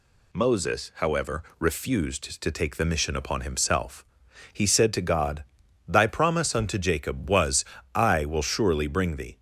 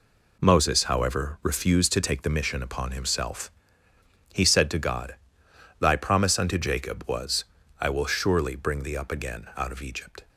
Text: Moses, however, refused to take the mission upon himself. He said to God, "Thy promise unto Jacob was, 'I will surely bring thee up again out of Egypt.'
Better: second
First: stops before "up again out of Egypt"; at 9.3 s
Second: none

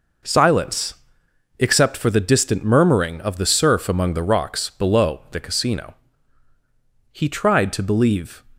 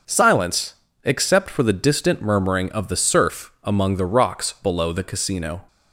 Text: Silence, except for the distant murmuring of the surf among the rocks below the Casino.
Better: second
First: goes on to say "He tried to believe"; from 7.1 s on; 1.3 s long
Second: none

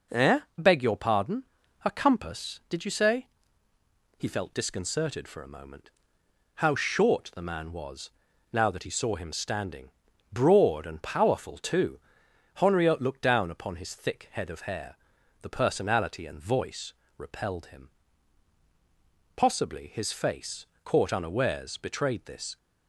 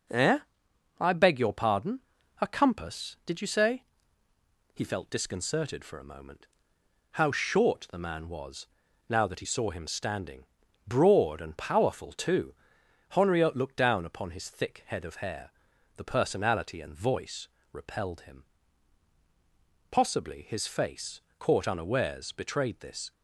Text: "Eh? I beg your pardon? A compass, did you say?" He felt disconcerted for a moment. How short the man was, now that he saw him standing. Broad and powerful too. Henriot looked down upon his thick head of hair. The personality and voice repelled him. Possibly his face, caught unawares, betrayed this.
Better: second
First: skips "I"; at 0.4 s // pauses between "voice" and "repelled"; slight; at 16.9 s; 0.24 s long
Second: pauses between "voice" and "repelled"; slight; at 17.4 s; 0.24 s long

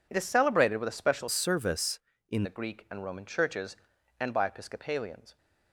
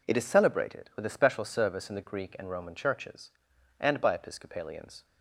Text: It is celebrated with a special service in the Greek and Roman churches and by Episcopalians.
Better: second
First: changes voice from "service" to "in"; from 1.2 to 2.4 s; 1.2 s long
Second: none

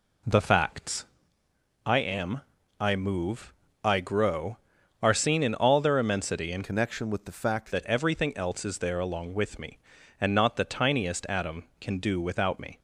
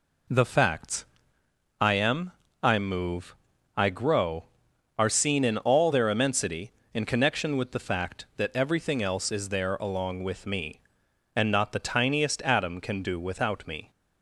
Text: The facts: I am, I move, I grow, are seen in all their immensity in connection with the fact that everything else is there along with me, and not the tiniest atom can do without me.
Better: second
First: changes voice from "connection" to "fact"; from 6.6 to 7.7 s; 1.1 s long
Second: none

